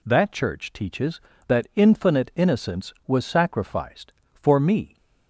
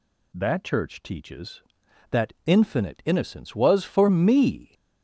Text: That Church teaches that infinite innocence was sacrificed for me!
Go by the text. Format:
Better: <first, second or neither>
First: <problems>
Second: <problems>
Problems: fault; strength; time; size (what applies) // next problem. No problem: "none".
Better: first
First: none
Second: skips "sacrificed"; at 3.8 s